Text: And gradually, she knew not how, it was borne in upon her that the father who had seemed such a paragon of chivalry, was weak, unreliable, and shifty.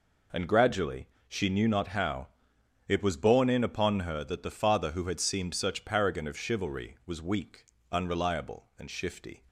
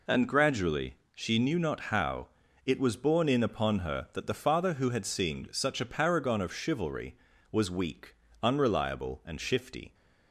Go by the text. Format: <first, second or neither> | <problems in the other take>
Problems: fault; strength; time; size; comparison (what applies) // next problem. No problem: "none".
second | skips "a"; at 5.8 s